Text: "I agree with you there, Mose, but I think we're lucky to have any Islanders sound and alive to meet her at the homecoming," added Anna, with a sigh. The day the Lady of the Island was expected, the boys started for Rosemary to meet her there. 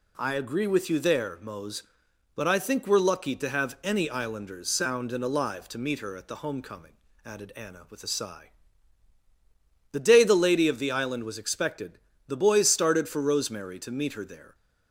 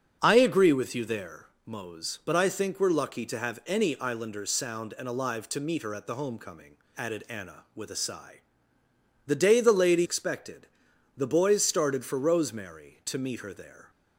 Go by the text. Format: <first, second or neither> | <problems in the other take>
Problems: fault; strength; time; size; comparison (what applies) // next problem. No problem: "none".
first | starts louder than the rest; until 1.2 s; 6.5 dB // skips "of the Island was"; at 10.0 s